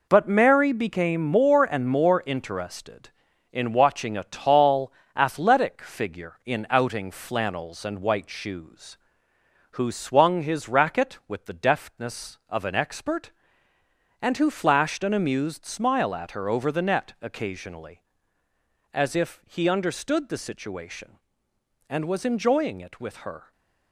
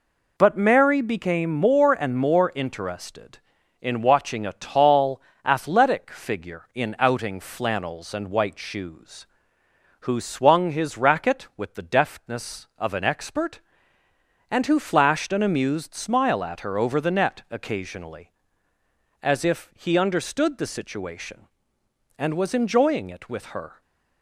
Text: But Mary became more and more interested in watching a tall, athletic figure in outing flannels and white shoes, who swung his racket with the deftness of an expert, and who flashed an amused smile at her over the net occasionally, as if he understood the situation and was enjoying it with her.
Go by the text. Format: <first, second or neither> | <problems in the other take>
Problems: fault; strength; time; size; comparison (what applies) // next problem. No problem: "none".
second | gets quieter; strong; throughout; 7.5 dB